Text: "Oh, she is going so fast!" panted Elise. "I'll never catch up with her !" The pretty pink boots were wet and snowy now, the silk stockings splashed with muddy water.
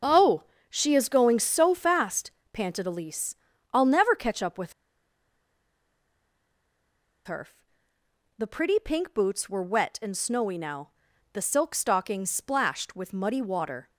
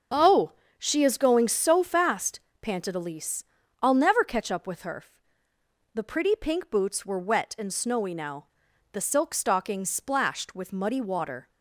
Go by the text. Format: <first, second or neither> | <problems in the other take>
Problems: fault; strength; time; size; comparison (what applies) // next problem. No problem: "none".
second | starts louder than the rest; until 1.3 s; 6.5 dB; also in the second // pauses between "with" and "her"; strong; at 4.7 s; 2.5 s long